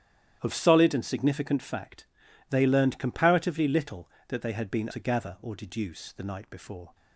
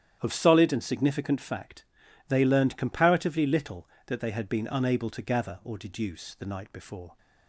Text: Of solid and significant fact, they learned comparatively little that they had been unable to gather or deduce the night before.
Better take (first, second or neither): second